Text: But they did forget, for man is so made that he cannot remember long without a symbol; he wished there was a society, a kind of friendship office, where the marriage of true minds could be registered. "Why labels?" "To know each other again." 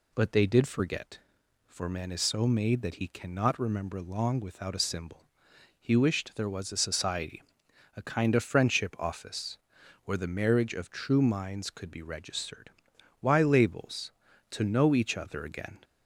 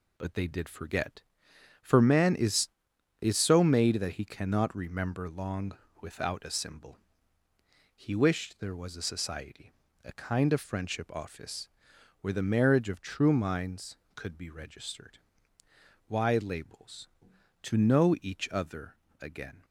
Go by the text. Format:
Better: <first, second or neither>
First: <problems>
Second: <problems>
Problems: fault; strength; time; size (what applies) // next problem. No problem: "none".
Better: first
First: none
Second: says "is" twice; at 3.2 s // pauses between "long" and "without"; slight; at 5.7 s; 0.24 s long // pauses between "other" and "again"; slight; at 18.9 s; 0.26 s long